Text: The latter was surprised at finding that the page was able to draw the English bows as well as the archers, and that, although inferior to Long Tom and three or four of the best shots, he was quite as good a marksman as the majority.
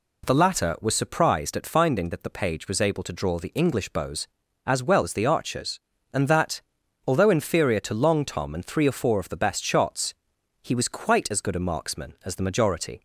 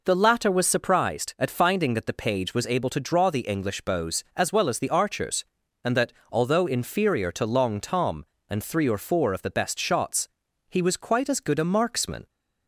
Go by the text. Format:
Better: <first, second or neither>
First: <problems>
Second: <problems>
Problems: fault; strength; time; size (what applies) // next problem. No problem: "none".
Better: first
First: none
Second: stops before "as the majority"; at 12.2 s